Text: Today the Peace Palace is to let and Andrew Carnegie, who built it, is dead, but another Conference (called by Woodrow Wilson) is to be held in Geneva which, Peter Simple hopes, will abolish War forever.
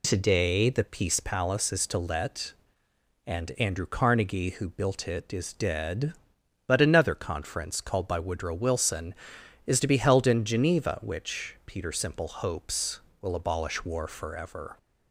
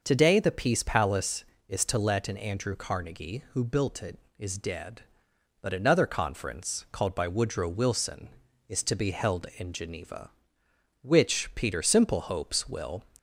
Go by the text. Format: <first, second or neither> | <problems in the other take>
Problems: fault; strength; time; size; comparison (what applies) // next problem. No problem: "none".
first | stops before "abolish War forever"; at 13.1 s